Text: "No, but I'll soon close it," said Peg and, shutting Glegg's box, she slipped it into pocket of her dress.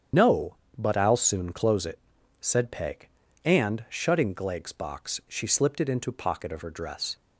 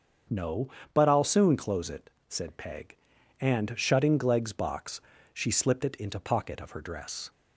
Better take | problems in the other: second | loses the start of "No"; at 0.1 s; 60 ms // starts louder than the rest; strong; until 1.3 s; 8 dB; strong in the second

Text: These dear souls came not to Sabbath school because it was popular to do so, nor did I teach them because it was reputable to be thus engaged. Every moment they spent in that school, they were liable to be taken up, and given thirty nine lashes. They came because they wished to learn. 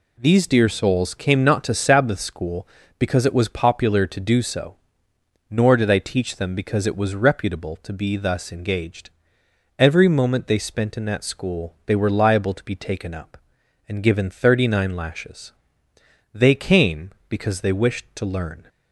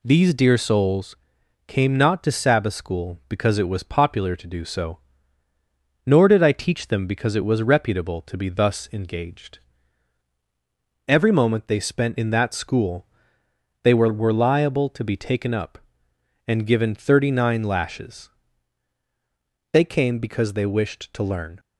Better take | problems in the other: first | pauses between "souls" and "came"; noticeable; at 1.1 s; 0.50 s long // says "were" twice; at 14.1 s

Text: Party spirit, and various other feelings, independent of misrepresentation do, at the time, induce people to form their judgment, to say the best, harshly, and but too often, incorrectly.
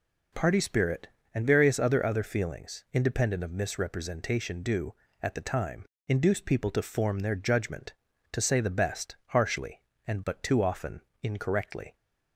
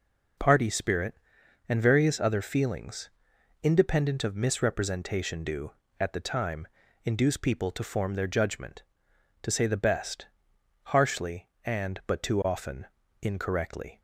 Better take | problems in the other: second | says "other" twice; at 2.0 s

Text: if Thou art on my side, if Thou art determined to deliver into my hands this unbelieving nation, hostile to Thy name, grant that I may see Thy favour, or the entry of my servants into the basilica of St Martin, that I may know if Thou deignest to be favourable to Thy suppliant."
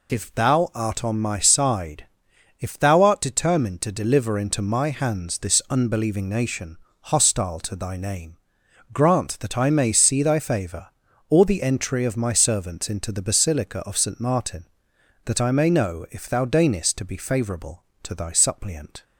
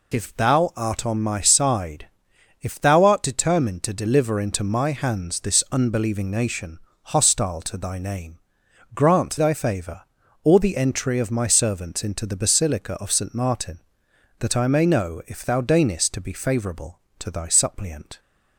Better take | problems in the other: first | skips "that I may see"; at 9.3 s

